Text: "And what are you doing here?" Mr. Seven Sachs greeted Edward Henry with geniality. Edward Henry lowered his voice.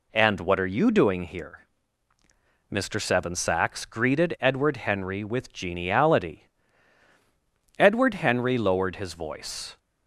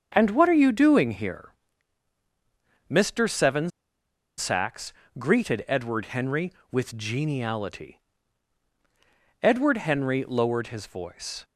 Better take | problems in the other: first | starts louder than the rest; strong; until 1.1 s; 7 dB // pauses between "Seven" and "Sachs"; noticeable; at 3.7 s; 0.67 s long // pauses between "Sachs" and "greeted"; slight; at 4.9 s; 0.24 s long

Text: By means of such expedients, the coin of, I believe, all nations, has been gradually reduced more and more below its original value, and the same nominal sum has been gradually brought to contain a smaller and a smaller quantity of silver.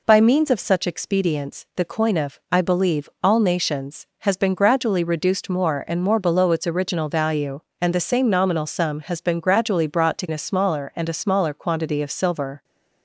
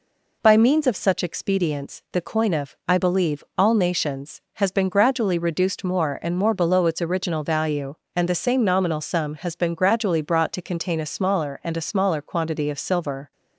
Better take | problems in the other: second | skips "contain"; at 10.2 s

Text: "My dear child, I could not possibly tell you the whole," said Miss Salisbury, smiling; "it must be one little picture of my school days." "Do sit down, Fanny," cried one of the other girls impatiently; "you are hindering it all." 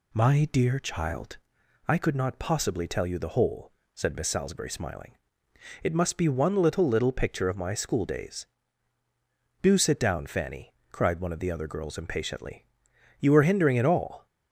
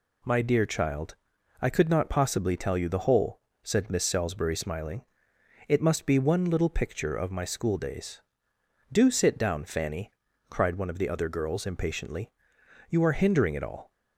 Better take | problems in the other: second | says "little" twice; at 6.8 s

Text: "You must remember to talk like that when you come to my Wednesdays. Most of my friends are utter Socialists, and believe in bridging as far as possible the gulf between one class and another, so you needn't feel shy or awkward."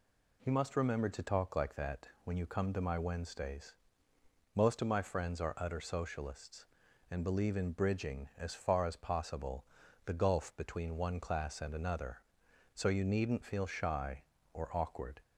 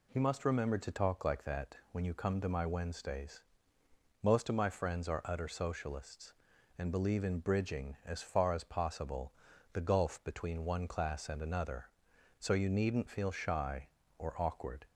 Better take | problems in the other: neither | pauses between "possible" and "the"; the same in both

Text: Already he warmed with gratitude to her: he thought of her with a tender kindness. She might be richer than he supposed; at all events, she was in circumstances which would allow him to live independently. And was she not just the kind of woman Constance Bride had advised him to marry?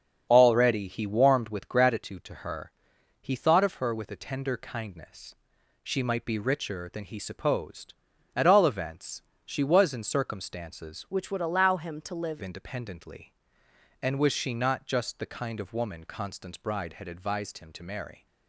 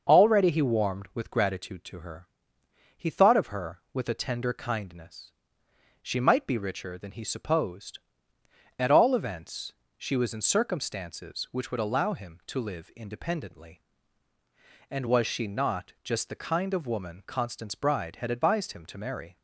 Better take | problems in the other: second | starts louder than the rest; strong; until 1.3 s; 7 dB; noticeable in the second // changes voice from "which" to "live"; from 11.1 to 12.4 s; 1.3 s long

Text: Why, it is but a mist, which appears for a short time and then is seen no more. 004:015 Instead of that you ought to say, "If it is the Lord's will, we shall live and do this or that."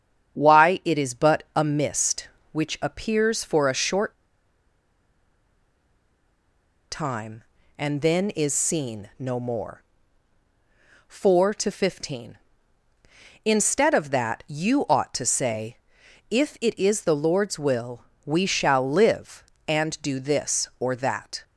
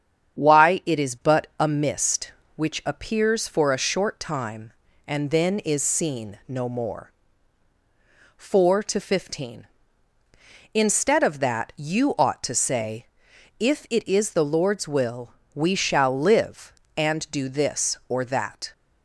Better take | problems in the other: second | starts louder than the rest; strong; until 1.4 s; 8.5 dB; strong in the second // pauses between "short" and "time"; strong; at 4.1 s; 2.7 s long

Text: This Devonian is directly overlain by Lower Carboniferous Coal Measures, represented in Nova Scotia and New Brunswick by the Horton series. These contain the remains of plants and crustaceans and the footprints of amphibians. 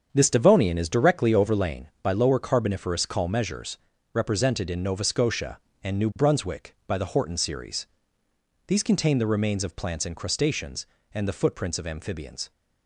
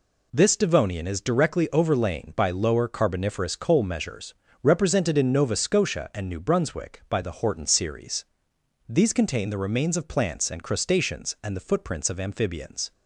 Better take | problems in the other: second | starts louder than the rest; strong; until 1.1 s; 7.5 dB // says "Call" for "Coal"; at 3.0 s

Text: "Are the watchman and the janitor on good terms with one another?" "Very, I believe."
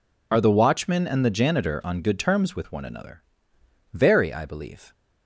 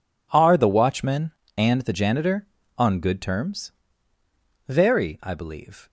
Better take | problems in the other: first | skips "with one another"; at 4.1 s

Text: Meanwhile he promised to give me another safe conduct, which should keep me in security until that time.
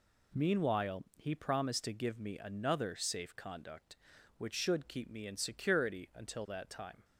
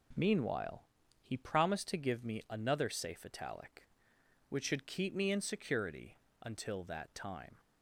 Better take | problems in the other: first | pauses between "Meanwhile" and "he"; at 0.8 s; 0.40 s long // says "italic" for "conduct"; at 3.2 s // pauses between "security" and "until"; slight; at 6.1 s; 0.28 s long

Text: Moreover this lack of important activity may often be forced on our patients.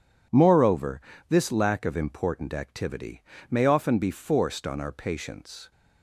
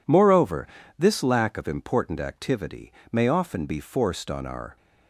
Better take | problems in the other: first | pauses between "Moreover" and "this"; slight; at 0.6 s; 0.30 s long; slight in the first // pauses between "activity" and "may"; slight; at 2.9 s; 0.20 s long; slight in the first // stops before "patients"; at 4.7 s

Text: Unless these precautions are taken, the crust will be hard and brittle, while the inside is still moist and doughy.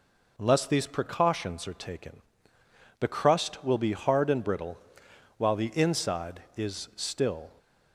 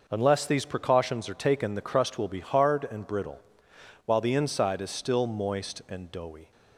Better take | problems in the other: second | stops before "moist and doughy"; at 7.5 s

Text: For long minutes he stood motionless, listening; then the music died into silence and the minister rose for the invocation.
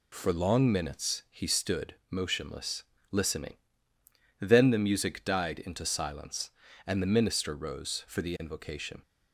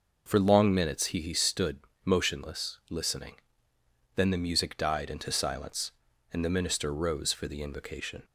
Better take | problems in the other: first | says "he" twice; at 1.2 s // pauses between "stood" and "motionless"; slight; at 1.7 s; 0.24 s long; slight in the first

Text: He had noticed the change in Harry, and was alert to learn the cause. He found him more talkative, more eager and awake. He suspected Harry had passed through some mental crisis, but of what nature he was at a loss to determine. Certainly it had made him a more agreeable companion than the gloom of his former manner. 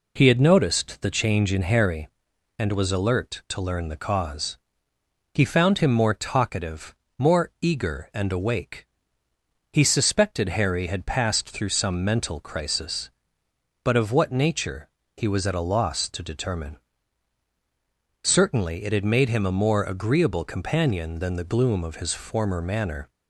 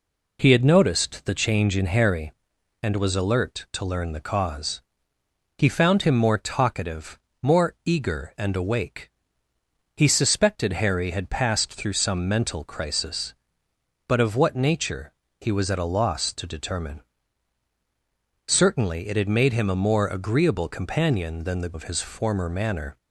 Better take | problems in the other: first | pauses between "nature" and "he"; slight; at 15.1 s; 0.28 s long; slight in the first // skips "gloom"; at 21.7 s

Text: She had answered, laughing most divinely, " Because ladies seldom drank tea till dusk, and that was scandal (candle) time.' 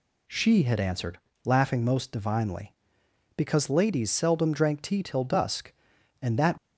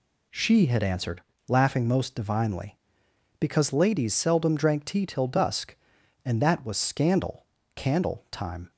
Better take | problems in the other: second | stops before "was scandal candle time"; at 6.5 s

